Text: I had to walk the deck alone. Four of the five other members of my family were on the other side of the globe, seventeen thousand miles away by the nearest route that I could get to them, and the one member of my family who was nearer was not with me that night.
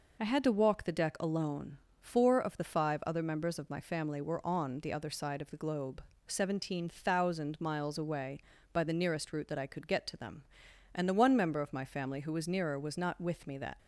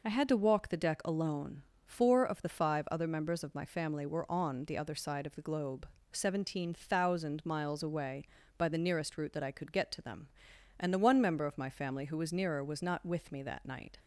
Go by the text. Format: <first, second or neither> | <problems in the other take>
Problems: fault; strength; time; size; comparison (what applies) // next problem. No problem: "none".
second | stops before "night"; at 13.7 s